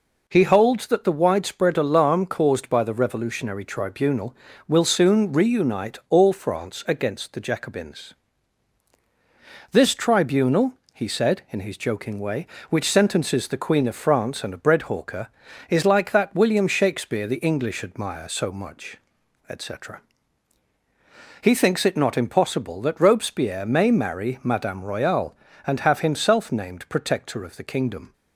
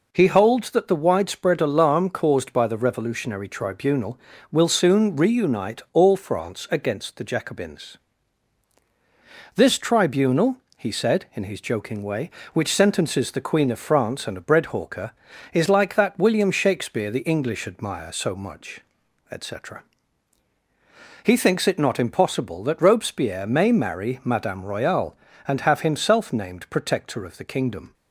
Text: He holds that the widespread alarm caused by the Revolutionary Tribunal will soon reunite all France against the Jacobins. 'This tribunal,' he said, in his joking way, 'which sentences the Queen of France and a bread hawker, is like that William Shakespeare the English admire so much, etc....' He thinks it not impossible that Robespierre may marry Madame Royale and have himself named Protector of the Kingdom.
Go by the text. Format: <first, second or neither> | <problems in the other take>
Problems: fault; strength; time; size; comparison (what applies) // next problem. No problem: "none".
neither | none